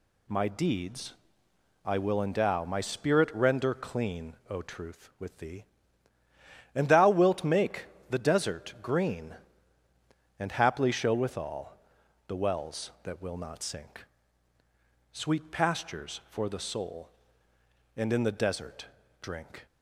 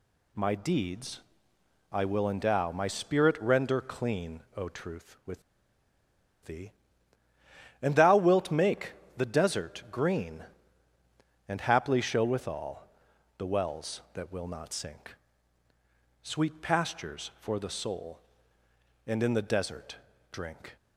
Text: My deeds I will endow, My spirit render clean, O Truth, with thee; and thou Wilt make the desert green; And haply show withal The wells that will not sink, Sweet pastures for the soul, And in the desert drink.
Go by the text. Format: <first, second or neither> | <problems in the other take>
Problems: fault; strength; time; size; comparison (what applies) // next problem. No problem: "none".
first | pauses between "deeds" and "I"; noticeable; at 1.1 s; 0.72 s long; noticeable in the first // pauses between "with" and "thee"; at 5.4 s; 1.0 s long // pauses between "make" and "the"; slight; at 8.9 s; 0.24 s long; slight in the first // pauses between "withal" and "The"; noticeable; at 12.8 s; 0.50 s long; noticeable in the first // pauses between "desert" and "drink"; slight; at 19.9 s; 0.34 s long; slight in the first